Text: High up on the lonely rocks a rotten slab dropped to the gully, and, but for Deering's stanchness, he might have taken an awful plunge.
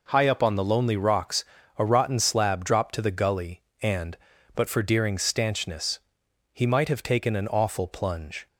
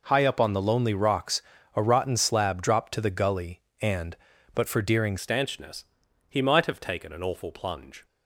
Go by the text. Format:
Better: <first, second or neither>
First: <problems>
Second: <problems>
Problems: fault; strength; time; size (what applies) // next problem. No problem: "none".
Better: first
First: pauses between "rocks" and "a"; slight; at 1.4 s; 0.34 s long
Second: pauses between "rocks" and "a"; slight; at 1.4 s; 0.34 s long // changes voice at "stanchness"; from 5.2 s on; 2.8 s long